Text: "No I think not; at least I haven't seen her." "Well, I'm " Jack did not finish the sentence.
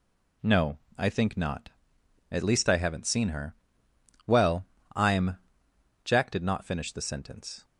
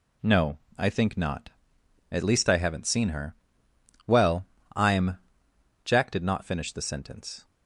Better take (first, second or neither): neither